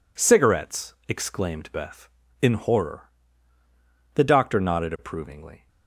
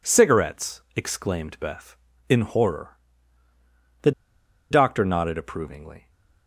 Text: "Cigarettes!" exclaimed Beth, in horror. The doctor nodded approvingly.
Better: first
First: none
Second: pauses between "The" and "doctor"; noticeable; at 4.1 s; 0.59 s long

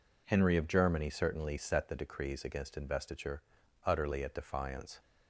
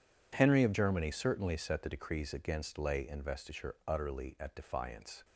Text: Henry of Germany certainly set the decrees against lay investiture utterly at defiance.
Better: second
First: skips "lay"; at 2.7 s // pauses between "investiture" and "utterly"; at 3.4 s; 0.42 s long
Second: none

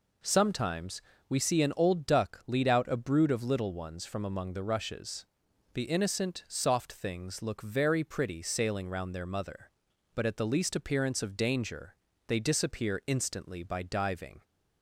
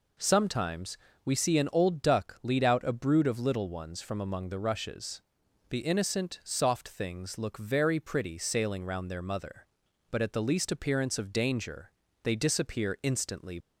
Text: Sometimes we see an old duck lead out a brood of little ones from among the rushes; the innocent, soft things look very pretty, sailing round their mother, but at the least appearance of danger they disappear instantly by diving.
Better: first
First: pauses between "Sometimes" and "we"; slight; at 1.0 s; 0.28 s long // pauses between "danger" and "they"; slight; at 11.9 s; 0.32 s long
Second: pauses between "Sometimes" and "we"; slight; at 0.9 s; 0.28 s long // pauses between "danger" and "they"; slight; at 11.9 s; 0.32 s long // stops before "by diving"; at 13.6 s

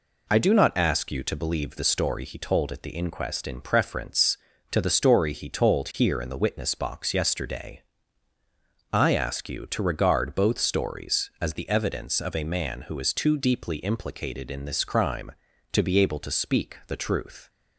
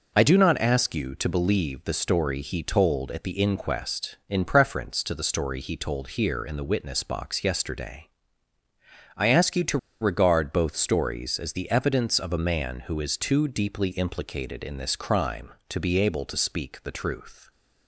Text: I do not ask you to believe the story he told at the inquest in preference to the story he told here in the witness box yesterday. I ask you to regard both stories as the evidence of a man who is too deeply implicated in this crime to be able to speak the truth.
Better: first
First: none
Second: pauses between "to" and "regard"; slight; at 9.7 s; 0.24 s long

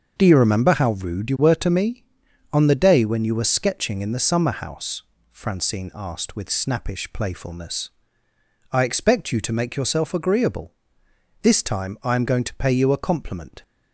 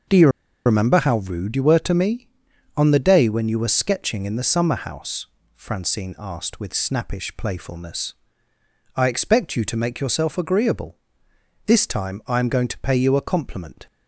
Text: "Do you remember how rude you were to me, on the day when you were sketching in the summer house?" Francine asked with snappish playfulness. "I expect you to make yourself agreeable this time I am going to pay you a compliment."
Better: first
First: starts louder than the rest; until 1.1 s; 6.5 dB // pauses between "agreeable" and "this"; noticeable; at 10.7 s; 0.70 s long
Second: starts louder than the rest; until 1.4 s; 6.5 dB // pauses between "you" and "remember"; at 0.2 s; 0.36 s long // pauses between "agreeable" and "this"; noticeable; at 10.9 s; 0.70 s long

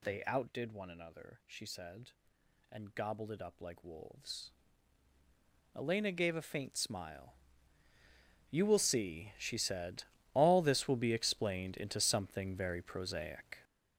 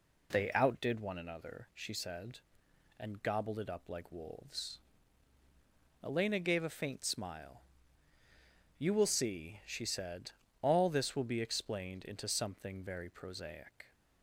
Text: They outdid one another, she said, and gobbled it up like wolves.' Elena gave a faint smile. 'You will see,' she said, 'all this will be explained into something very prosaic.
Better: second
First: gets louder; strong; throughout; 9.5 dB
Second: none

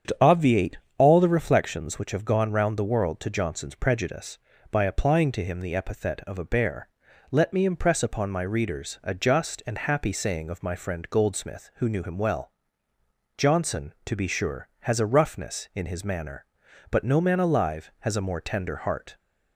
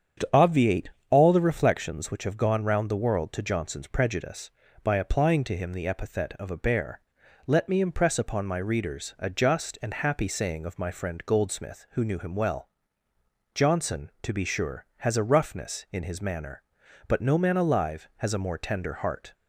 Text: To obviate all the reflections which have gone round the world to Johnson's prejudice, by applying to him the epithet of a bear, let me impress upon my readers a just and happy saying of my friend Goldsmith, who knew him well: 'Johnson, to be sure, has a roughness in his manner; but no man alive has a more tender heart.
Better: neither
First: starts louder than the rest; strong; until 1.3 s; 8 dB // pauses between "obviate" and "all"; slight; at 0.7 s; 0.20 s long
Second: starts louder than the rest; strong; until 1.4 s; 8 dB // pauses between "obviate" and "all"; slight; at 0.9 s; 0.20 s long

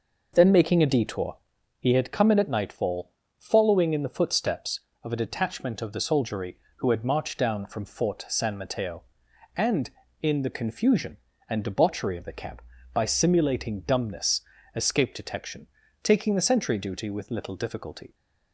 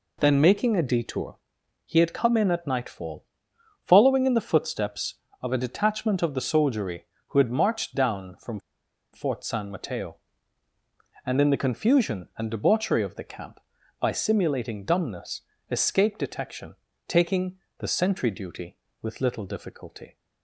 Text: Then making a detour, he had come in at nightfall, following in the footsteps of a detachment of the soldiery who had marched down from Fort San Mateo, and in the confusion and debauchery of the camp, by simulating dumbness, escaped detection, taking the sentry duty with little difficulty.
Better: first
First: none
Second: pauses between "from" and "Fort"; noticeable; at 8.5 s; 0.53 s long // pauses between "taking" and "the"; slight; at 17.5 s; 0.22 s long

